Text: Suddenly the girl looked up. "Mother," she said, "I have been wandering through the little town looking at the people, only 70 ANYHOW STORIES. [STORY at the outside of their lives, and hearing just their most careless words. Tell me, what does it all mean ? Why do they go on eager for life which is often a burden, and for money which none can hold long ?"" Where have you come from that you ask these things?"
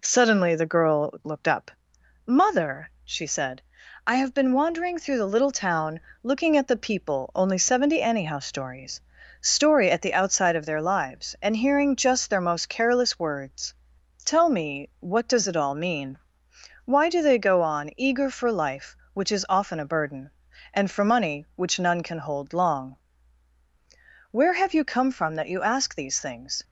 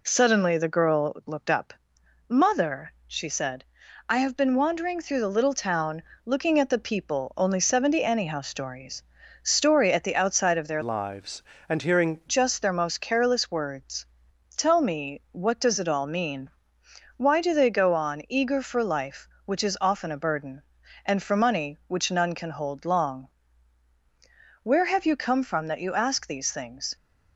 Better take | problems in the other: first | pauses between "town" and "looking"; slight; at 6.0 s; 0.22 s long; slight in the first // changes voice from "lives" to "hearing"; from 10.8 to 12.2 s; 1.4 s long

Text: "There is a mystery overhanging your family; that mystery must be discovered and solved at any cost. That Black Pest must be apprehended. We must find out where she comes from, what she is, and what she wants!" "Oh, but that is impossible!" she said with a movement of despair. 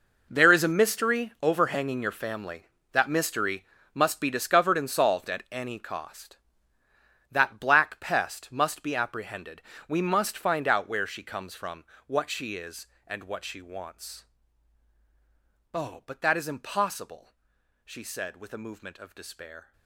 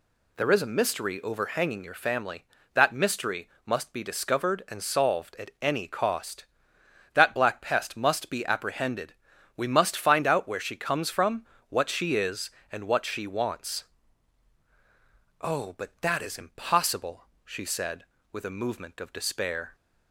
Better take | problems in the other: second | gets quieter; strong; throughout; 15 dB // pauses between "mystery" and "must"; slight; at 3.6 s; 0.30 s long; slight in the second

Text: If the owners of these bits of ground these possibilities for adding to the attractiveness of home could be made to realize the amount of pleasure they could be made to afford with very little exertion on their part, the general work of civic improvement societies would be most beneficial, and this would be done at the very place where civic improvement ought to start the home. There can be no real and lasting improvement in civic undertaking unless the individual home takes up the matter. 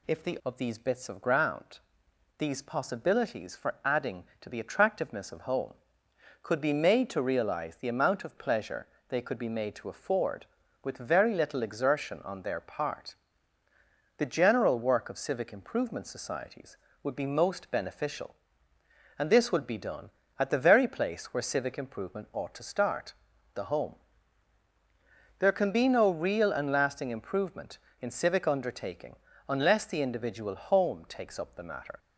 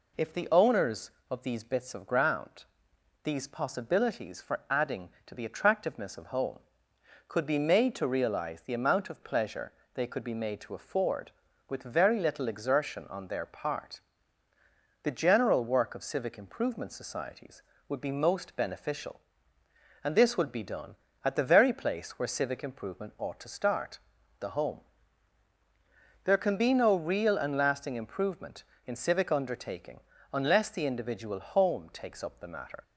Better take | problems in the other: second | skips "owners"; at 0.4 s // pauses between "ground" and "these"; noticeable; at 1.8 s; 0.58 s long; noticeable in the second // pauses between "pleasure" and "they"; slight; at 8.8 s; 0.22 s long; slight in the second // pauses between "start" and "the"; at 23.1 s; 0.40 s long; also in the second // pauses between "undertaking" and "unless"; slight; at 29.1 s; 0.32 s long; slight in the second

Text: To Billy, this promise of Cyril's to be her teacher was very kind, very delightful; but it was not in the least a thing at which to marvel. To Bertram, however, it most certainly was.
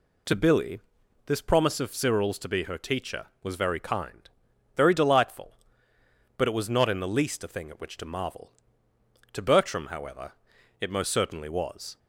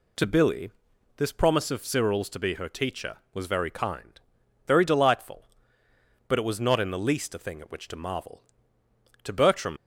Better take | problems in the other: first | stops before "however it most certainly was"; at 9.7 s

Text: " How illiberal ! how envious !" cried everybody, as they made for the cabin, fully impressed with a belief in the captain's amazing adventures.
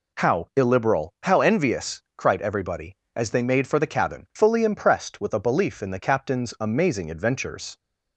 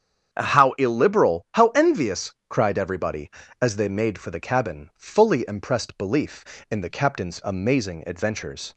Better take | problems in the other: first | starts louder than the rest; strong; until 1.4 s; 8 dB // skips "with a"; at 5.9 s

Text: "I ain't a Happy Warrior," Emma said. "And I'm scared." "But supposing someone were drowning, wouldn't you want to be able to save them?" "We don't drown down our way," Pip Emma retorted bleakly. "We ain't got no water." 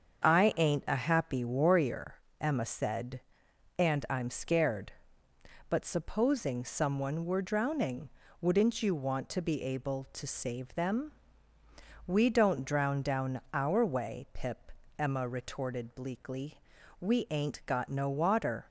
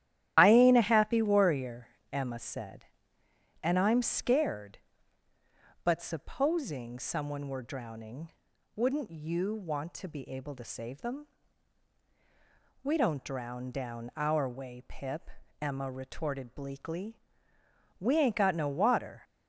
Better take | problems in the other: first | loses the start of "I"; at 0.3 s; 55 ms // starts louder than the rest; strong; until 1.3 s; 12.5 dB; also in the first // pauses between "Pip" and "Emma"; slight; at 15.3 s; 0.32 s long; slight in the first

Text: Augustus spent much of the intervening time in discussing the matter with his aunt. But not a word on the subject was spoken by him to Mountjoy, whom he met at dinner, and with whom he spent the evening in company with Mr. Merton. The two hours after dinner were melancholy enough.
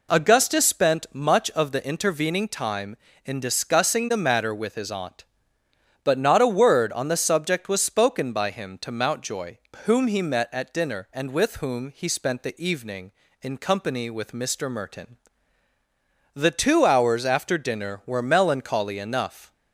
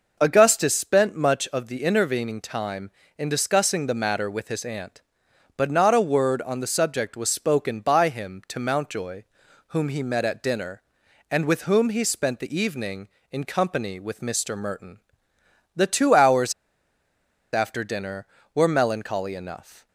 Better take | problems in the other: first | pauses between "hours" and "after"; at 16.5 s; 1.0 s long

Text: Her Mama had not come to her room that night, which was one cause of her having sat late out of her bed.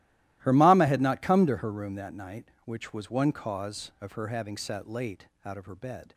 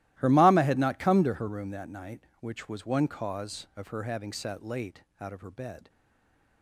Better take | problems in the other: first | starts louder than the rest; strong; until 1.2 s; 16 dB; strong in the first // pauses between "late" and "out"; slight; at 5.0 s; 0.16 s long; slight in the first // stays silent after the last word; slight; from 5.8 s on; 0.8 s long

